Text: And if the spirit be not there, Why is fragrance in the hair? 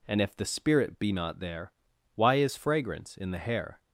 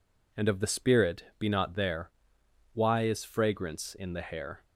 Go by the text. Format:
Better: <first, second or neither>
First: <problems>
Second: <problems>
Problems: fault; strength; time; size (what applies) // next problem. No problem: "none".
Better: first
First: none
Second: says "of" for "if"; at 0.4 s